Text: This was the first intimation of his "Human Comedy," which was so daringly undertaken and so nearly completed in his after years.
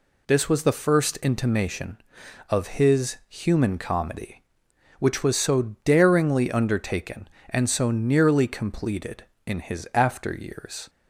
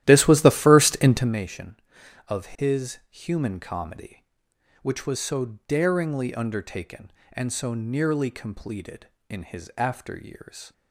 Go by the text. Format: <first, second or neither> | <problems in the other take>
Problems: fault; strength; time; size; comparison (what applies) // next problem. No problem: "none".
first | starts louder than the rest; strong; until 1.4 s; 13 dB